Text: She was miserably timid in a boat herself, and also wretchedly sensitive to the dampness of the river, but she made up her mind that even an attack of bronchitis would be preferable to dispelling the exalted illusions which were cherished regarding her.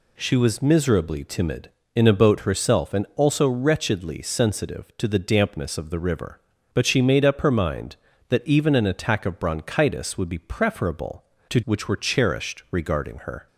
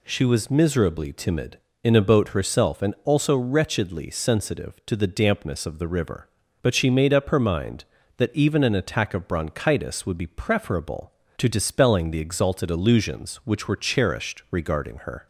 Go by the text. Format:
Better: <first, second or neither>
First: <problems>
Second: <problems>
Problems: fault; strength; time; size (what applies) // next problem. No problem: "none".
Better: second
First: skips "dispelling the exalted illusions"; at 11.6 s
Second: none